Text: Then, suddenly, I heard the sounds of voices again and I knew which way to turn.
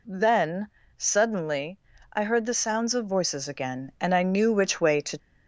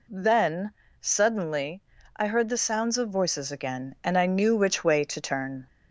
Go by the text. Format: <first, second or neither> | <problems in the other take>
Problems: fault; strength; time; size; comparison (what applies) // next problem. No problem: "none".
second | stops before "turn"; at 5.1 s